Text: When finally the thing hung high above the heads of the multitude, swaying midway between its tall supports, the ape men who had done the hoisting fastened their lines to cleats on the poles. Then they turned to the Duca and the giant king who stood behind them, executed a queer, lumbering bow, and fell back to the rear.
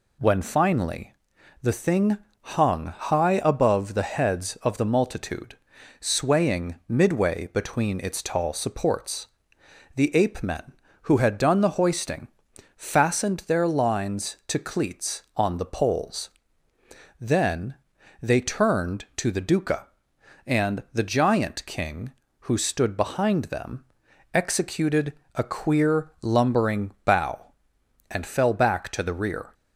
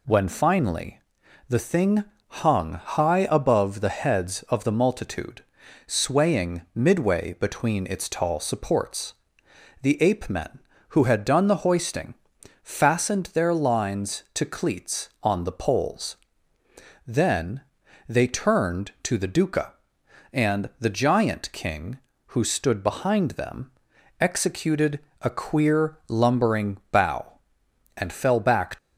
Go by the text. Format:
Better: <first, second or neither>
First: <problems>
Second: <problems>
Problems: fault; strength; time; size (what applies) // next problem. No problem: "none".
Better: first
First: pauses between "finally" and "the"; noticeable; at 1.1 s; 0.48 s long // pauses between "thing" and "hung"; slight; at 2.1 s; 0.24 s long // pauses between "hoisting" and "fastened"; noticeable; at 12.2 s; 0.48 s long // pauses between "Then" and "they"; noticeable; at 17.7 s; 0.46 s long // pauses between "executed" and "a"; slight; at 25.1 s; 0.22 s long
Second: pauses between "finally" and "the"; noticeable; at 0.9 s; 0.48 s long // pauses between "thing" and "hung"; slight; at 2.0 s; 0.24 s long // pauses between "hoisting" and "fastened"; noticeable; at 12.1 s; 0.48 s long // pauses between "Then" and "they"; noticeable; at 17.6 s; 0.46 s long // pauses between "executed" and "a"; slight; at 24.9 s; 0.22 s long // stops before "to the rear"; at 28.7 s